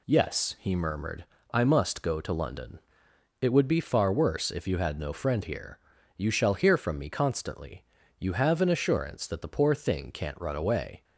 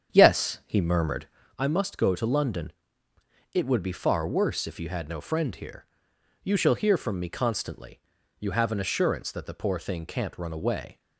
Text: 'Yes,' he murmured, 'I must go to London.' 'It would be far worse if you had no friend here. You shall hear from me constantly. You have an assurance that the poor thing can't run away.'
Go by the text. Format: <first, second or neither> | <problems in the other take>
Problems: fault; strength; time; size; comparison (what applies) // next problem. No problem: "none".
first | starts louder than the rest; strong; until 1.6 s; 8 dB